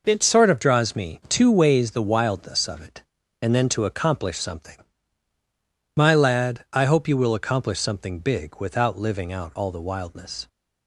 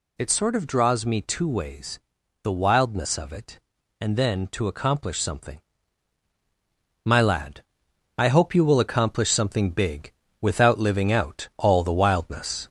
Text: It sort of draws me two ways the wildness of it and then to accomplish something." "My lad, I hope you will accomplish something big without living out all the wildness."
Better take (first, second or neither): first